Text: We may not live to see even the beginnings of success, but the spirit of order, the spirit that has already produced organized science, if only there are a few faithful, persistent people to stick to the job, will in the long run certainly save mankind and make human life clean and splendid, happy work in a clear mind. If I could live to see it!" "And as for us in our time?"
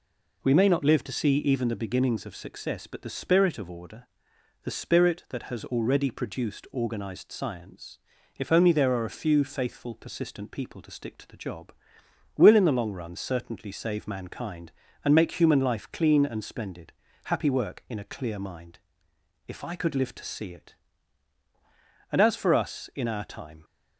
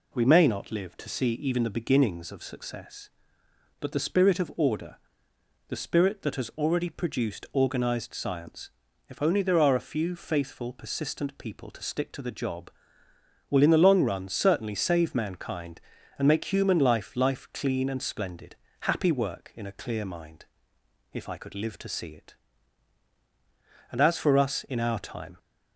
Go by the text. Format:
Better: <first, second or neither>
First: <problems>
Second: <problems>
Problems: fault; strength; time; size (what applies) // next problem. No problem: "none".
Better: first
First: none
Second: says "life" twice; at 17.1 s